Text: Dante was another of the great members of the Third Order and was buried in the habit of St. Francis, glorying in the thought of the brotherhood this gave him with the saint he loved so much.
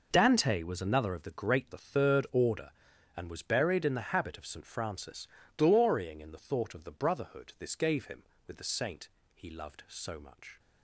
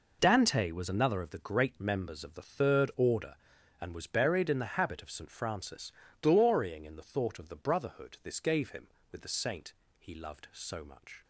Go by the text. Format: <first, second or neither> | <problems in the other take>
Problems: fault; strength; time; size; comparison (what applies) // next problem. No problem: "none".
second | skips "members of"; at 1.7 s // pauses between "saint" and "he"; slight; at 9.0 s; 0.26 s long; slight in the second